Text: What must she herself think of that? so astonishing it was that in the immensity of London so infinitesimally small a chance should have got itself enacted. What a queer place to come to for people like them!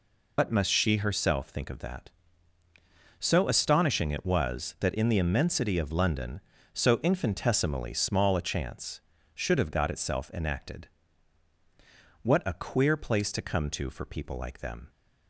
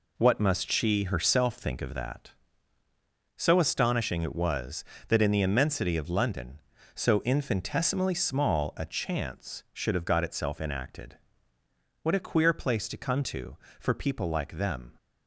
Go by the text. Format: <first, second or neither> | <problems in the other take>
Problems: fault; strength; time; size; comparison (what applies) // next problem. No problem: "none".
second | loses the start of "What"; at 0.3 s; 110 ms